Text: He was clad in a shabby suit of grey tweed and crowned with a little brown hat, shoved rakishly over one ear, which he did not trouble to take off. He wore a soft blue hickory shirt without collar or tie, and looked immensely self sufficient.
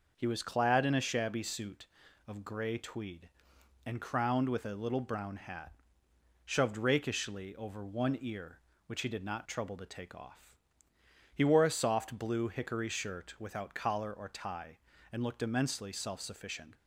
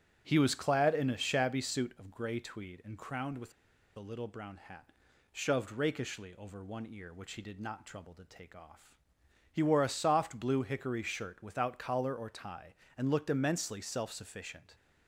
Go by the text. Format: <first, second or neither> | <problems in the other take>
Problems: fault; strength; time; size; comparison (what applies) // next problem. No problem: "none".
first | starts louder than the rest; strong; until 1.2 s; 8 dB // pauses between "with" and "a"; at 3.5 s; 0.44 s long